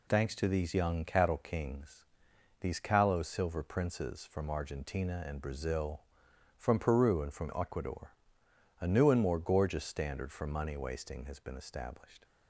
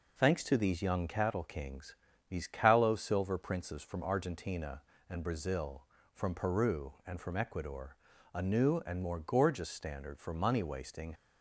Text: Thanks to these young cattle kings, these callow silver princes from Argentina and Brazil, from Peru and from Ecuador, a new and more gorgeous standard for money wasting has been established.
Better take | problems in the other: first | stops before "has been established"; at 11.1 s

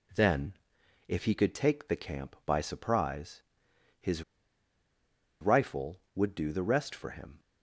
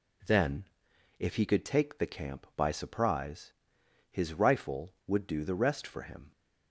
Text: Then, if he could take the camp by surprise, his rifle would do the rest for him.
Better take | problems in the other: second | pauses between "his" and "rifle"; at 4.2 s; 1.1 s long

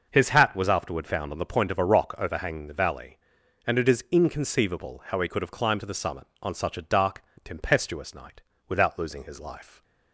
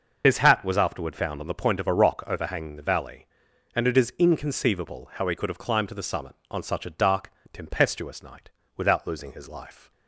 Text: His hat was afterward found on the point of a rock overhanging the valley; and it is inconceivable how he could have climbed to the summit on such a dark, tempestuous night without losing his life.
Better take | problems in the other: first | loses the start of "His"; at 0.2 s; 65 ms // starts louder than the rest; noticeable; until 1.2 s; 6 dB // pauses between "night" and "without"; slight; at 8.4 s; 0.28 s long; slight in the first

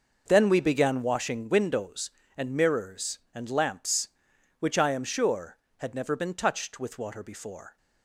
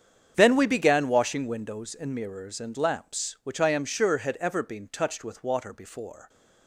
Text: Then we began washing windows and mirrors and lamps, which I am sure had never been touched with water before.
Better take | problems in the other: first | starts louder than the rest; strong; until 1.3 s; 7.5 dB // says "ever" for "never"; at 4.4 s

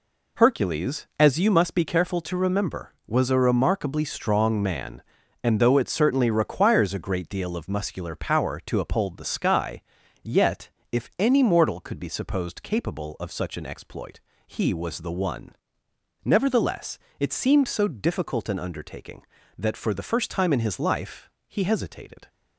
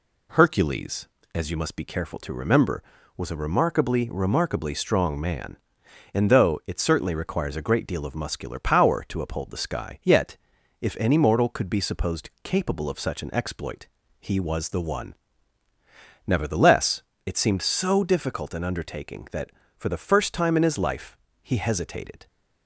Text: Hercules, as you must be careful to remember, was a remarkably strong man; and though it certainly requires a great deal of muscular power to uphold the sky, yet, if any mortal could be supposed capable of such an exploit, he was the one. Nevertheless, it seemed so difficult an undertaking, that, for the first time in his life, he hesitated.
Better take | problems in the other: first | says "remarkably" twice; at 4.1 s

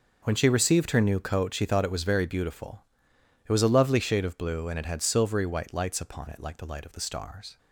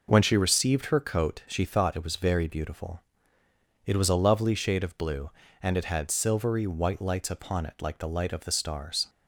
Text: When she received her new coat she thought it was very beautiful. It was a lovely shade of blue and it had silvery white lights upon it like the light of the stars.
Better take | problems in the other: first | skips "new"; at 0.9 s

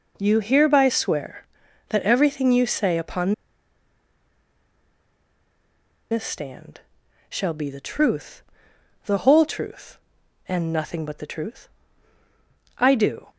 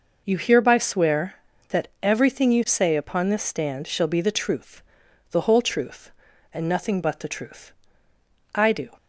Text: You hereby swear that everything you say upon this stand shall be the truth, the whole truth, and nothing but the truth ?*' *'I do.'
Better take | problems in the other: second | pauses between "upon" and "this"; strong; at 3.3 s; 2.7 s long // pauses between "stand" and "shall"; noticeable; at 6.8 s; 0.48 s long

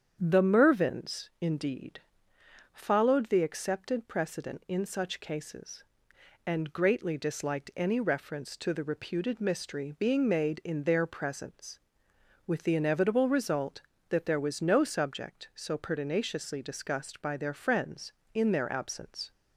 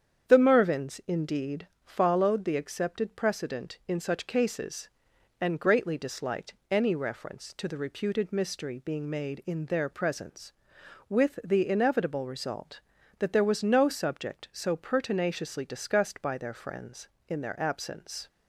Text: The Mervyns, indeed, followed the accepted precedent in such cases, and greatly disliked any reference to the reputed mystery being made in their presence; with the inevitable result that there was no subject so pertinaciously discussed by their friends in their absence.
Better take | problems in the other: neither | starts louder than the rest; strong; the same in both

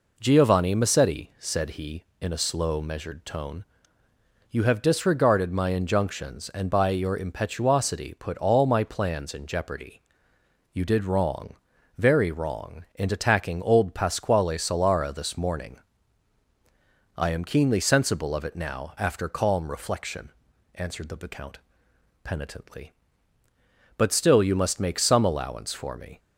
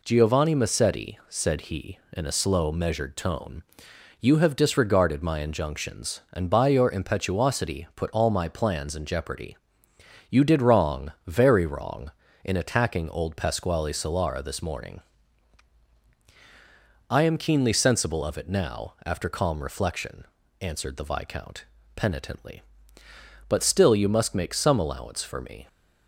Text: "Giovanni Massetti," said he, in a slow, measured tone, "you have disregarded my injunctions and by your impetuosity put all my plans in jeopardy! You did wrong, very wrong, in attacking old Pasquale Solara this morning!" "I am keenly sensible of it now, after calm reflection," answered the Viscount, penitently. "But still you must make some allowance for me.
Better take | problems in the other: neither | none

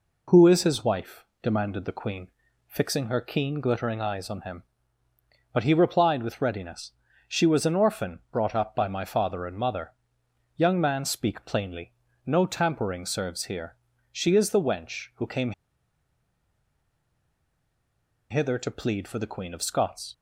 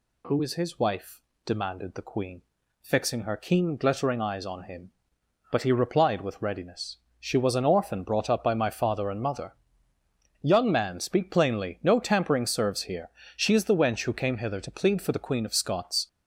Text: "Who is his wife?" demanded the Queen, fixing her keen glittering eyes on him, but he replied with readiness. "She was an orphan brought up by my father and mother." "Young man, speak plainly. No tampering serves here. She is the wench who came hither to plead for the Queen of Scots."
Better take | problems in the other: second | pauses between "came" and "hither"; strong; at 15.5 s; 2.7 s long

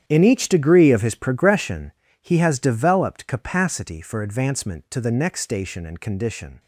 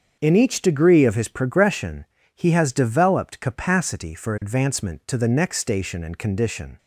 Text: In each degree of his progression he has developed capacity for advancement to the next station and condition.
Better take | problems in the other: second | gets quieter; strong; throughout; 14.5 dB // starts louder than the rest; strong; until 1.0 s; 9.5 dB; also in the second // pauses between "progression" and "he"; slight; at 1.9 s; 0.30 s long; slight in the second

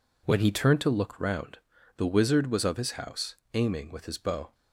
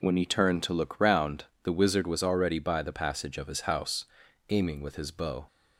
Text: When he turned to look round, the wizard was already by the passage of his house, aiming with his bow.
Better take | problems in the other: second | skips "already by the passage"; at 2.6 s

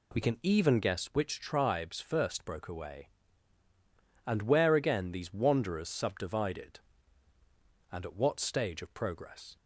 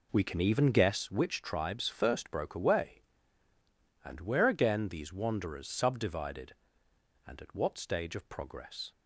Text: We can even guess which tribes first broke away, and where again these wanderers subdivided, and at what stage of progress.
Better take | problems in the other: first | starts louder than the rest; until 1.2 s; 3.5 dB

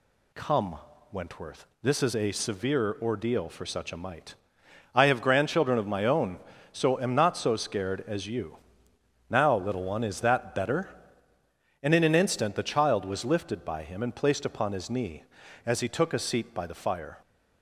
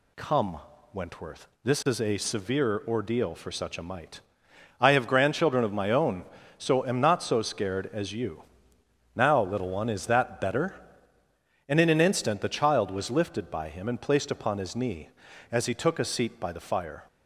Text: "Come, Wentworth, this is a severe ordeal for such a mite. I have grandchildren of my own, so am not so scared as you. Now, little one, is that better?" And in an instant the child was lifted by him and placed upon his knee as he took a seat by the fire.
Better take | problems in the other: neither | none

